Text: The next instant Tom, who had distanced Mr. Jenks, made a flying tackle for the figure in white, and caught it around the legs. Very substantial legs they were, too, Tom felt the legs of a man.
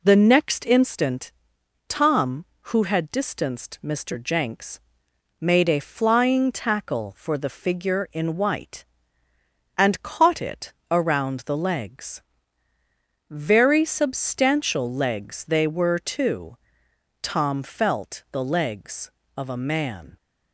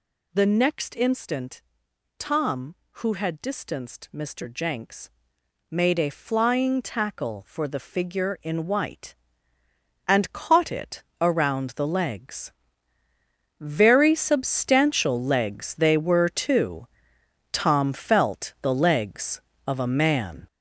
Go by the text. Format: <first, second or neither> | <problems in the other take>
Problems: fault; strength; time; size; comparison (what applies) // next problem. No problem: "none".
first | gets louder; strong; throughout; 7.5 dB // pauses between "instant" and "Tom"; noticeable; at 1.6 s; 0.56 s long; noticeable in the first // pauses between "it" and "around"; slight; at 11.0 s; 0.18 s long; slight in the first